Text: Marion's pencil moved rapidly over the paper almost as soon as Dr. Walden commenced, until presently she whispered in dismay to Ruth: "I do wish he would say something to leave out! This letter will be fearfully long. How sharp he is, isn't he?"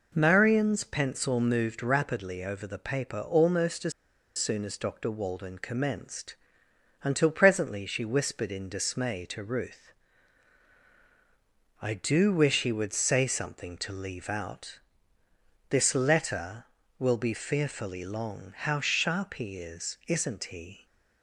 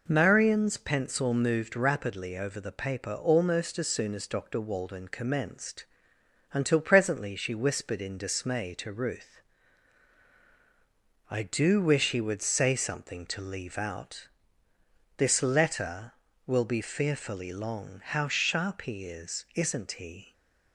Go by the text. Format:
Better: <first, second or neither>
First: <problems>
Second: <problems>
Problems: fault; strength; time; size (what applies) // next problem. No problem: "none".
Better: second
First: pauses between "as" and "soon"; noticeable; at 3.9 s; 0.46 s long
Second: none